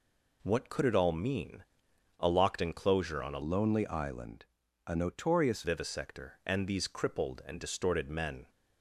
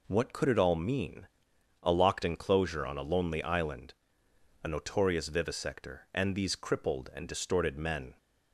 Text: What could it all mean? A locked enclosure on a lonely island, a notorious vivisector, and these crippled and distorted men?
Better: second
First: changes voice from "lonely" to "notorious"; from 3.4 to 5.6 s; 2.2 s long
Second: none

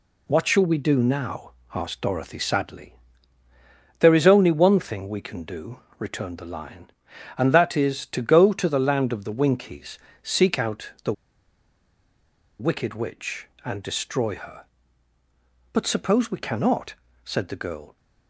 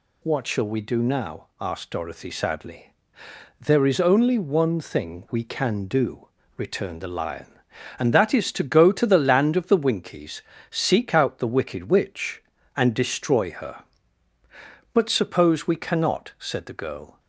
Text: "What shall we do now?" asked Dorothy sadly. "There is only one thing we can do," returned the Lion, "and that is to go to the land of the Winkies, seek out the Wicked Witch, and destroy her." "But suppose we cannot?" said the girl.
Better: second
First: pauses between "the" and "Wicked"; strong; at 11.1 s; 1.4 s long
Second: none

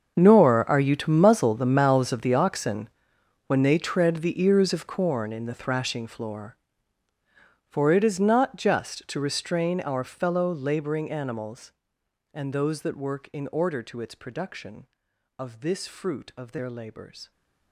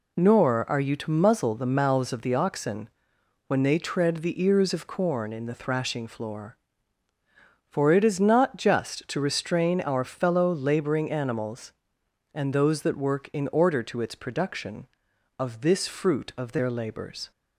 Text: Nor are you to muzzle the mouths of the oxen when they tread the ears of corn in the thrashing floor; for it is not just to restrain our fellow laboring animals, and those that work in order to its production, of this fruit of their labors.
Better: second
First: gets quieter; strong; throughout; 18 dB // pauses between "oxen" and "when"; noticeable; at 2.8 s; 0.58 s long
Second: pauses between "oxen" and "when"; noticeable; at 2.8 s; 0.58 s long

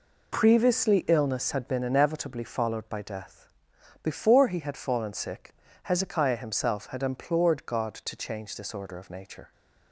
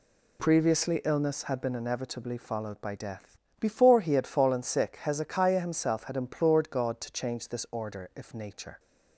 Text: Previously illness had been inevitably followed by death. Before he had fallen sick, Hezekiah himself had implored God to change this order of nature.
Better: first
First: none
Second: says "if" for "of"; at 8.1 s

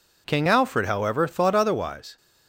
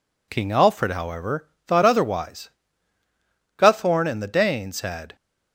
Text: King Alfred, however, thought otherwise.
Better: first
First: none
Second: goes on to say "Guthorn and the Danes had"; from 3.5 s on; 1.5 s long

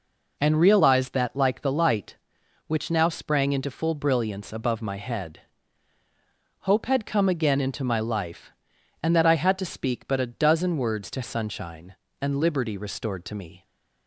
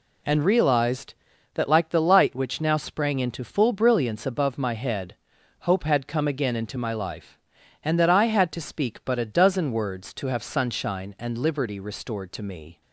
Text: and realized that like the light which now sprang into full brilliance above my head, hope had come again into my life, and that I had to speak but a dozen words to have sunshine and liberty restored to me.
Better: second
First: skips "have"; at 11.2 s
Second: none

